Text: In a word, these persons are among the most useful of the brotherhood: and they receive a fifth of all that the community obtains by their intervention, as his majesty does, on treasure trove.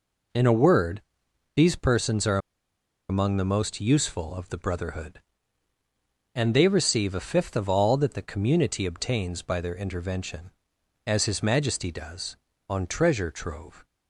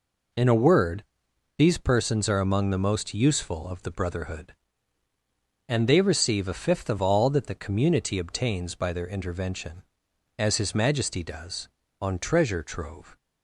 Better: second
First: pauses between "are" and "among"; noticeable; at 2.3 s; 0.71 s long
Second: none

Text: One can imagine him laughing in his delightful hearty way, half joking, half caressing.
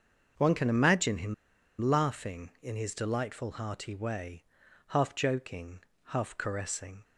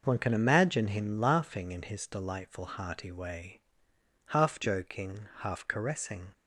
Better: second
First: starts louder than the rest; until 1.8 s; 6.5 dB // pauses between "him" and "laughing"; noticeable; at 1.3 s; 0.46 s long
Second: none

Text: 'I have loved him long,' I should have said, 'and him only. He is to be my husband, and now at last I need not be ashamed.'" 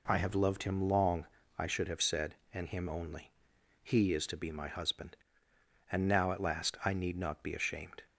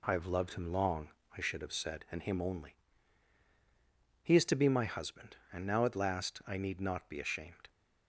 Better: neither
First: none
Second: none

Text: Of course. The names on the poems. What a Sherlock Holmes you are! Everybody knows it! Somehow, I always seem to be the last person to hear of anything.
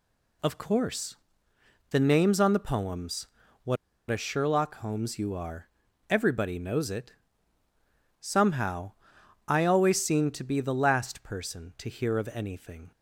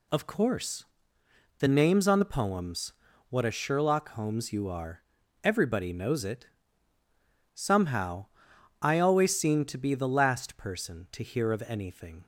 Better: second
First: pauses between "What" and "a"; slight; at 3.7 s; 0.34 s long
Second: none

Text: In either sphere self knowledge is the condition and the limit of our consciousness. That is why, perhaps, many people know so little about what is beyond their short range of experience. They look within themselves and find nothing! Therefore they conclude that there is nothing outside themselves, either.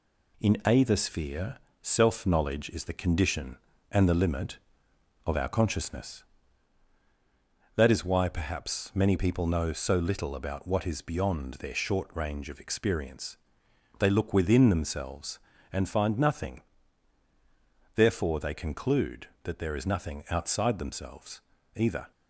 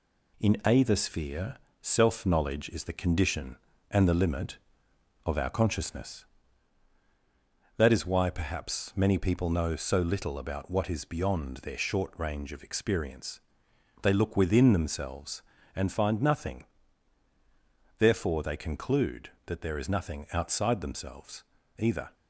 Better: neither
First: pauses between "sphere" and "self"; slight; at 1.5 s; 0.24 s long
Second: pauses between "sphere" and "self"; slight; at 1.5 s; 0.24 s long

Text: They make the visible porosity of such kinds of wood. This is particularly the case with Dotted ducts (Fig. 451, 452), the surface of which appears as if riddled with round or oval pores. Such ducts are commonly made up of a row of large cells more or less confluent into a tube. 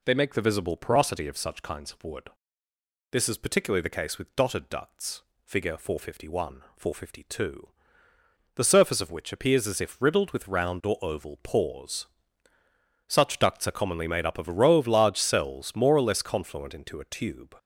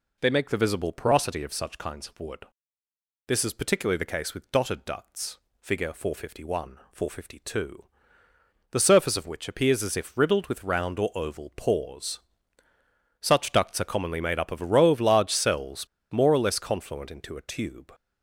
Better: first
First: none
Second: pauses between "cells" and "more"; slight; at 15.8 s; 0.25 s long

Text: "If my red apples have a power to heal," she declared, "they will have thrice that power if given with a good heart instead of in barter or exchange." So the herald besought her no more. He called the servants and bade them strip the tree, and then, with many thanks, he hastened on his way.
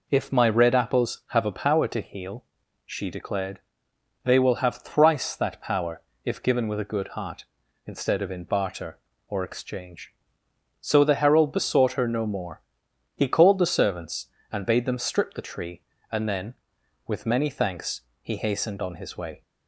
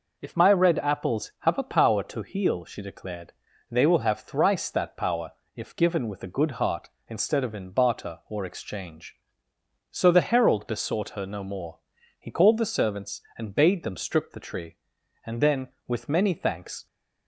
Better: first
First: pauses between "power" and "if"; slight; at 6.0 s; 0.22 s long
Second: pauses between "power" and "if"; slight; at 5.3 s; 0.24 s long // stops before "he hastened on his way"; at 16.8 s

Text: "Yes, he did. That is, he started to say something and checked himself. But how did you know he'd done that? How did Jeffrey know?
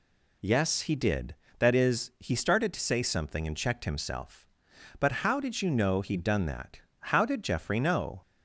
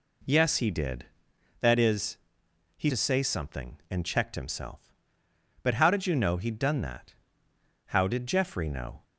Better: first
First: none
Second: skips "started"; at 2.8 s

